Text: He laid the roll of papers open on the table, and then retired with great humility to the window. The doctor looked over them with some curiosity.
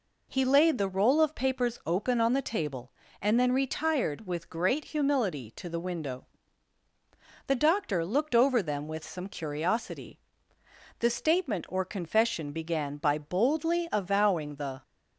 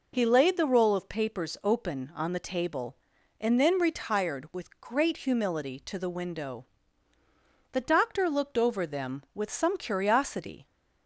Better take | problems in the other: second | goes on to say "The statement or confession began by boldly avowing the"; strong; from 10.9 s on; 3.8 s long

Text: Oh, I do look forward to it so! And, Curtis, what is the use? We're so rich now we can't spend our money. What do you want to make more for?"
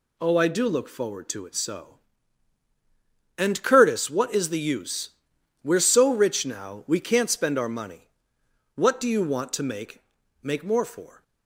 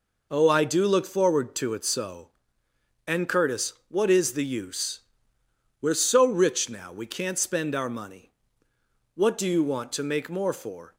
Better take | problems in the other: second | says "make" twice; at 10.4 s

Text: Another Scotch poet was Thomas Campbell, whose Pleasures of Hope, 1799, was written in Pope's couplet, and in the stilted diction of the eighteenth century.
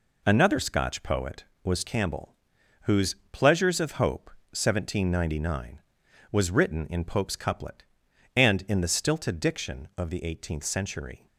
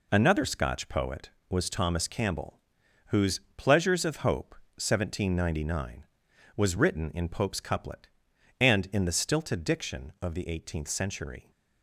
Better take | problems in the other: second | skips "Thomas"; at 1.8 s // pauses between "whose" and "Pleasures"; slight; at 3.1 s; 0.16 s long; slight in the second

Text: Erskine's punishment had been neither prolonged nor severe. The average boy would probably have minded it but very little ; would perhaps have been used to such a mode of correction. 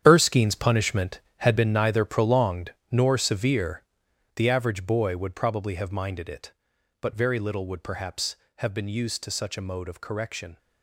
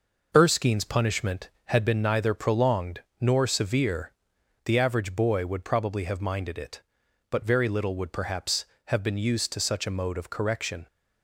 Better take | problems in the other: second | gets quieter; strong; throughout; 11.5 dB // pauses between "prolonged" and "nor"; slight; at 2.7 s; 0.16 s long; slight in the second

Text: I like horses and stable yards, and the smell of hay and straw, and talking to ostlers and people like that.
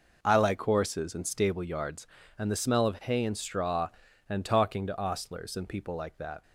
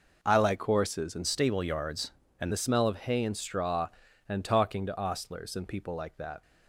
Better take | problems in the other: first | changes voice from "stable" to "and"; from 1.2 to 2.5 s; 1.3 s long

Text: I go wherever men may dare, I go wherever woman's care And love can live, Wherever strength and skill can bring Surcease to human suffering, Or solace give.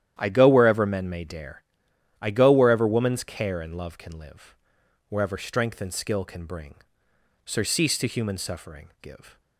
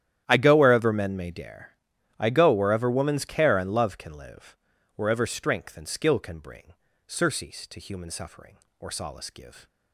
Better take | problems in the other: second | starts louder than the rest; strong; until 1.1 s; 10.5 dB; strong in the second // pauses between "bring" and "Surcease"; noticeable; at 6.7 s; 0.68 s long; slight in the second // skips "Or solace"; at 8.9 s

